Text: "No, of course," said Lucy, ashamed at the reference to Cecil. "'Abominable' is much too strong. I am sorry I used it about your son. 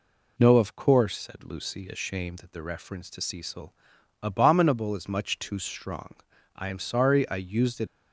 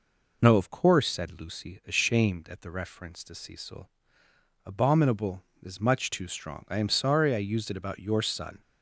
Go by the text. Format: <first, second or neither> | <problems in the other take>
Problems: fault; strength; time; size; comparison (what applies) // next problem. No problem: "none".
second | stops before "about your son"; at 7.8 s